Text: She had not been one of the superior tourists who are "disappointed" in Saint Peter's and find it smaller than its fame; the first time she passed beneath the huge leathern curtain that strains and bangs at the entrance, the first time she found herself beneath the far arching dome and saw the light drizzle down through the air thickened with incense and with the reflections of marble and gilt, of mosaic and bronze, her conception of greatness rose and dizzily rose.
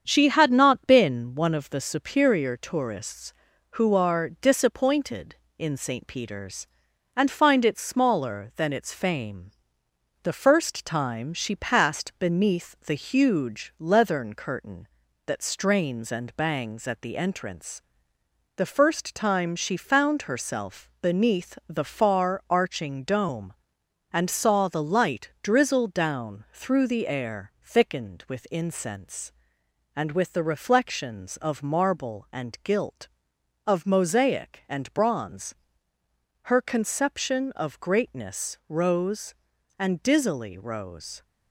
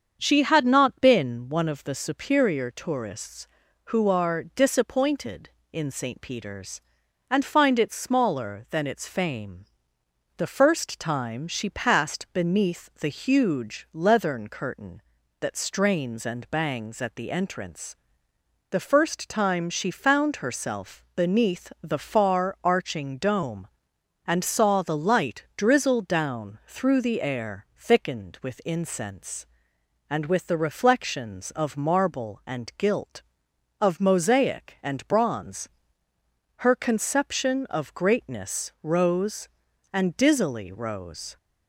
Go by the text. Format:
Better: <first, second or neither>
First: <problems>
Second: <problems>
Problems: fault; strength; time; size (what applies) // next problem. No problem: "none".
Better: second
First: gets quieter; noticeable; throughout; 4 dB // starts louder than the rest; strong; until 1.0 s; 7.5 dB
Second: starts louder than the rest; strong; until 1.2 s; 7 dB